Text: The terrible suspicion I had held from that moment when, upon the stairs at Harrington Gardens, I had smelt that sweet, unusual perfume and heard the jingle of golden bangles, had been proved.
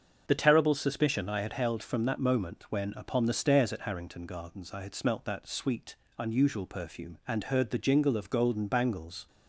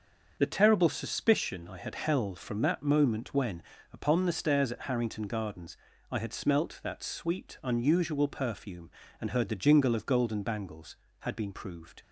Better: second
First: starts louder than the rest; until 1.3 s; 7 dB // stops before "had been proved"; at 9.2 s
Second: starts louder than the rest; until 1.4 s; 6.5 dB

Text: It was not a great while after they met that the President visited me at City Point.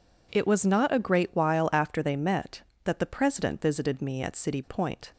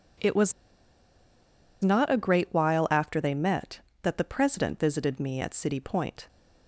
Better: first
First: none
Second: pauses between "was" and "not"; strong; at 0.5 s; 1.2 s long

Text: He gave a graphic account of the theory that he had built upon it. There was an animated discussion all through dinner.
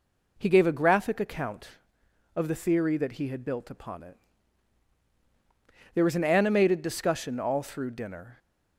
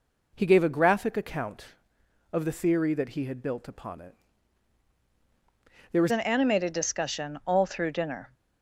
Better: first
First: none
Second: changes voice at "an"; from 6.0 s on; 2.3 s long

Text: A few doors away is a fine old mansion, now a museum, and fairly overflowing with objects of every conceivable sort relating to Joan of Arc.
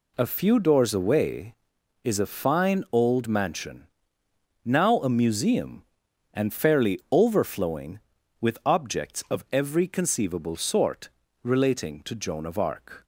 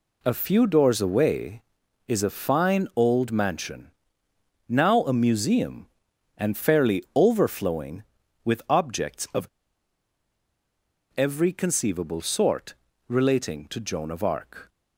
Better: first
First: pauses between "sort" and "relating"; slight; at 11.0 s; 0.34 s long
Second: pauses between "of" and "every"; strong; at 9.4 s; 1.6 s long // pauses between "sort" and "relating"; slight; at 12.7 s; 0.34 s long

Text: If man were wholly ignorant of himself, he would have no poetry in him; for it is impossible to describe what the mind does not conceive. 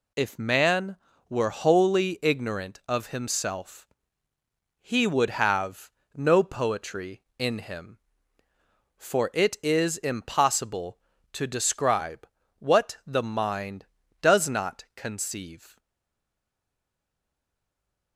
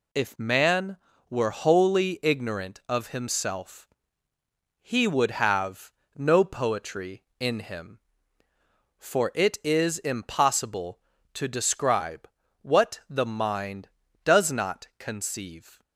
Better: second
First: pauses between "have" and "no"; slight; at 5.9 s; 0.26 s long // pauses between "describe" and "what"; slight; at 12.2 s; 0.32 s long // stays silent after the last word; from 15.7 s on; 2.4 s long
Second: pauses between "have" and "no"; slight; at 5.9 s; 0.26 s long // pauses between "describe" and "what"; slight; at 12.2 s; 0.34 s long

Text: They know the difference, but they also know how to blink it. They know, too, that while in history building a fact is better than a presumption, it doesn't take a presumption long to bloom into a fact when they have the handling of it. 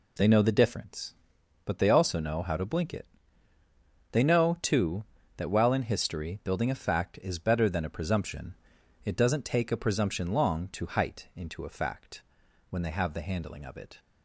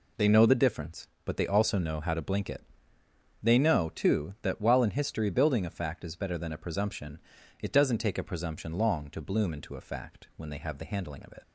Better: second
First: says "height" for "bloom"; at 10.8 s // pauses between "fact" and "when"; noticeable; at 12.2 s; 0.48 s long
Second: none

